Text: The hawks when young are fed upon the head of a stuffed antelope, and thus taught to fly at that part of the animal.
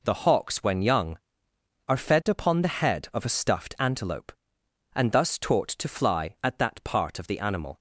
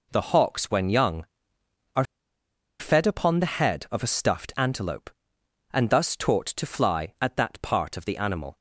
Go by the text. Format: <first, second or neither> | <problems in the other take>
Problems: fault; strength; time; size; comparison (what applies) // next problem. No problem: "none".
first | pauses between "are" and "fed"; noticeable; at 2.0 s; 0.75 s long